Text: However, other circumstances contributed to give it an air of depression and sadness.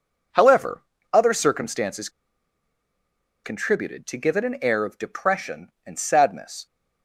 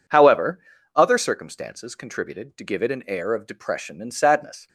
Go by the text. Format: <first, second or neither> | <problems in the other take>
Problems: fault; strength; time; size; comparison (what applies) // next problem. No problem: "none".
second | pauses between "circumstances" and "contributed"; strong; at 2.0 s; 1.3 s long